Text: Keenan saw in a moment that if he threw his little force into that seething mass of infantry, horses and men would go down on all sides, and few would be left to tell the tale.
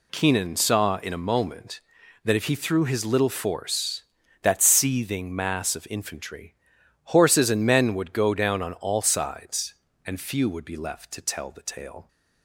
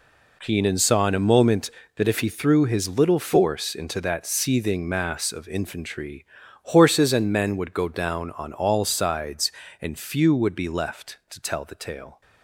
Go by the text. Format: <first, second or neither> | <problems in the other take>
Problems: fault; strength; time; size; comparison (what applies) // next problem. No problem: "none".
second | skips "into"; at 4.2 s